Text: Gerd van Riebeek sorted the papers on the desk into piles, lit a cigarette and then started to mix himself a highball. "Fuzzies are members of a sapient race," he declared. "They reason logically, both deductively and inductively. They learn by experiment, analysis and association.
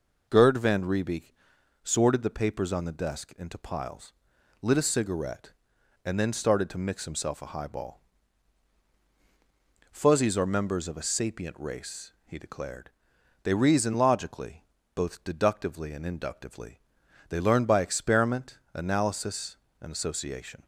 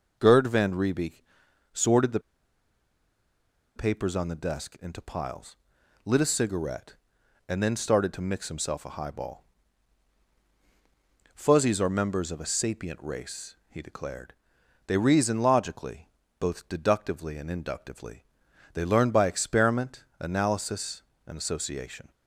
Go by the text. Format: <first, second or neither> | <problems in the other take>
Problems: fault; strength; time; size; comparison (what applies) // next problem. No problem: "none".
first | pauses between "Riebeek" and "sorted"; noticeable; at 1.2 s; 0.52 s long; noticeable in the first // pauses between "the" and "papers"; strong; at 2.1 s; 1.5 s long